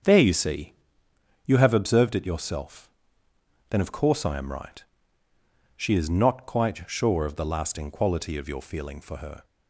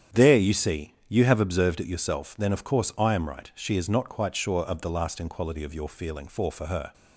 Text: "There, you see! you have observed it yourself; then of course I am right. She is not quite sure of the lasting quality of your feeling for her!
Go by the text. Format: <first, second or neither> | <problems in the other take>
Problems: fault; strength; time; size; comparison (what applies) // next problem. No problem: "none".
first | starts louder than the rest; strong; until 1.2 s; 8.5 dB; strong in the first // says "for" twice; at 6.5 s